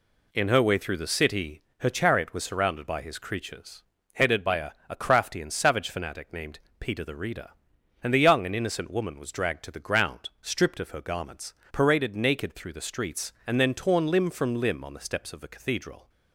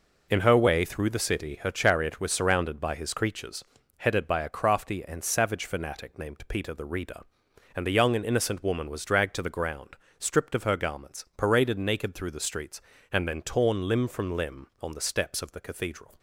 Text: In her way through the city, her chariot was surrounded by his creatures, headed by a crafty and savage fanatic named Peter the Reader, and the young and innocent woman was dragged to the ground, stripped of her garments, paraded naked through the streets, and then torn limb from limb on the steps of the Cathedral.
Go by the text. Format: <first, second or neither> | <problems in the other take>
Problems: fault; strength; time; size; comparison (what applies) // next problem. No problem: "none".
second | says "a" twice; at 4.8 s // pauses between "named" and "Peter"; slight; at 6.6 s; 0.18 s long